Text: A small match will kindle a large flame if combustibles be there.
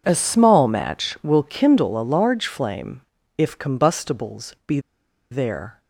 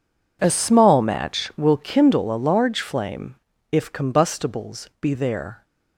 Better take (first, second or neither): second